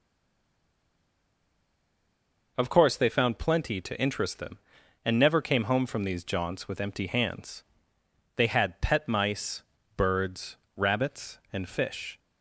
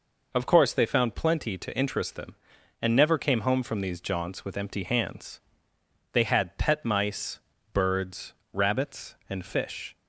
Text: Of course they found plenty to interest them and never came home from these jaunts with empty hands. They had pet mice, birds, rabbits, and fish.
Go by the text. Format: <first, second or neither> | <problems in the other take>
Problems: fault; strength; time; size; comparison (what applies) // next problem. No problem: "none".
second | stays silent before the first word; strong; until 2.5 s; 2.5 s long